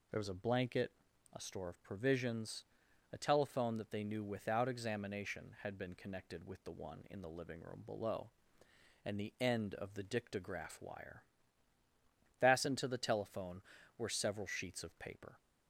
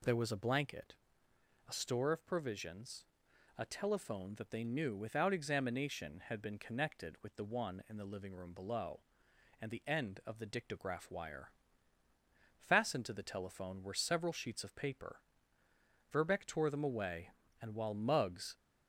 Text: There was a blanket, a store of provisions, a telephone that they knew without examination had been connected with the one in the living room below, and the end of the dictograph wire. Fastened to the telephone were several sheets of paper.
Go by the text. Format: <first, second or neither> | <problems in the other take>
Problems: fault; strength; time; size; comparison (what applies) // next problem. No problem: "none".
first | goes on to say "Verbeck tore them away and while Muggs"; strong; from 16.1 s on; 2.4 s long